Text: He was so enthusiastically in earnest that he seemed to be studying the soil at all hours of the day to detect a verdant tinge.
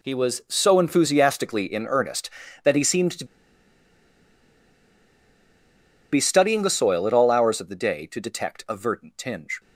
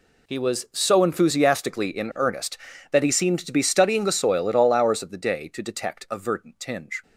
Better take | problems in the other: second | pauses between "to" and "be"; strong; at 3.2 s; 2.8 s long

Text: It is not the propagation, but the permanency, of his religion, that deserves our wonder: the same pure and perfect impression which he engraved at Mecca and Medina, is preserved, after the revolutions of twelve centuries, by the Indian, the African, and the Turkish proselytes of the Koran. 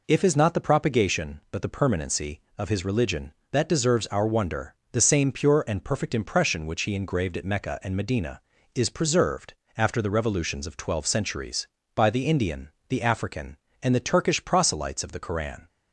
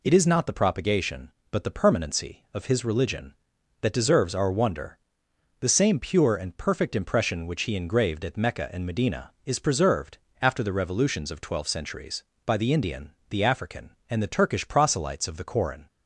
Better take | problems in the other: second | says "If" for "It"; at 0.0 s

